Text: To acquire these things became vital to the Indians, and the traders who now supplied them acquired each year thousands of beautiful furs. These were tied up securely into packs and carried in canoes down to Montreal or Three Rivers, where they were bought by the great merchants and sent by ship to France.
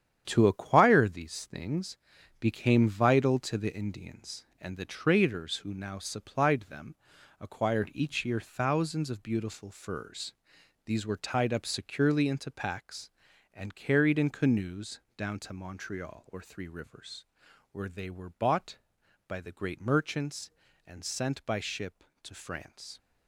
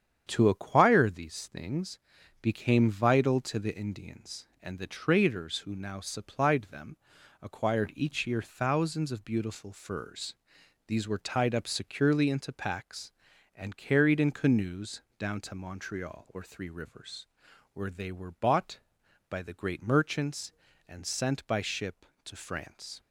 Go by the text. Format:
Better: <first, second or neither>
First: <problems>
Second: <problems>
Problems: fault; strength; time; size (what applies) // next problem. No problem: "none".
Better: second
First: gets quieter; strong; throughout; 8.5 dB // starts louder than the rest; strong; until 1.2 s; 9 dB // pauses between "things" and "became"; at 1.9 s; 0.44 s long // pauses between "them" and "acquired"; at 6.9 s; 0.44 s long // pauses between "canoes" and "down"; slight; at 14.9 s; 0.16 s long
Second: starts louder than the rest; strong; until 1.2 s; 8.5 dB // pauses between "things" and "became"; at 1.9 s; 0.44 s long // pauses between "them" and "acquired"; at 6.9 s; 0.44 s long // pauses between "canoes" and "down"; slight; at 15.0 s; 0.16 s long